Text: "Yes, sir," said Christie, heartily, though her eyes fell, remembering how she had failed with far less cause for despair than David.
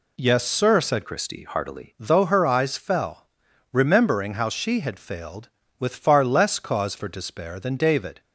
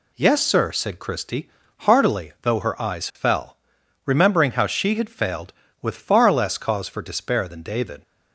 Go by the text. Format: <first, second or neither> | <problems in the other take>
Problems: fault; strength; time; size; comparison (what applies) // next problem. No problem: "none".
second | changes voice from "Christie" to "heartily"; from 1.0 to 1.9 s; 0.9 s long